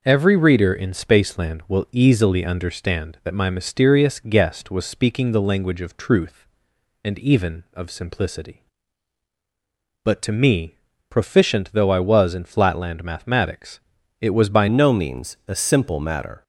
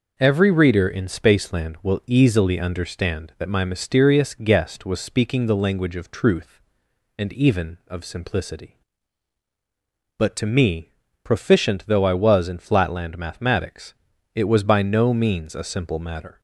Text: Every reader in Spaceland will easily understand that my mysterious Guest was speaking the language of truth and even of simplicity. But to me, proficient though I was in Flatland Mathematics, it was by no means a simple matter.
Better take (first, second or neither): second